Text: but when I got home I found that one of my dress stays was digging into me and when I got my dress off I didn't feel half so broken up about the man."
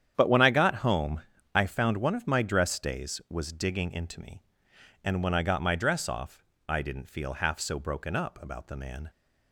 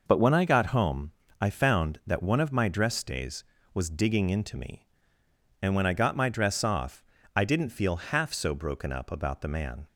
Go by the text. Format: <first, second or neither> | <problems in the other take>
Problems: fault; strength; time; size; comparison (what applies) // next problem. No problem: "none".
second | starts louder than the rest; strong; until 1.1 s; 9 dB // pauses between "home" and "I"; slight; at 1.2 s; 0.32 s long; slight in the second // skips "that"; at 1.9 s // pauses between "off" and "I"; slight; at 6.4 s; 0.24 s long; slight in the second